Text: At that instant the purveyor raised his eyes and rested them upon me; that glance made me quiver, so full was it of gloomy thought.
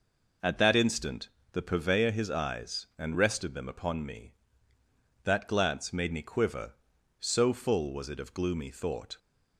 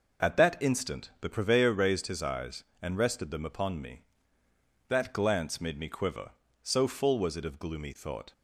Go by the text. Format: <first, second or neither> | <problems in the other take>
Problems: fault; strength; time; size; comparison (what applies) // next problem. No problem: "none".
second | pauses between "instant" and "the"; slight; at 1.2 s; 0.24 s long // skips "raised"; at 2.1 s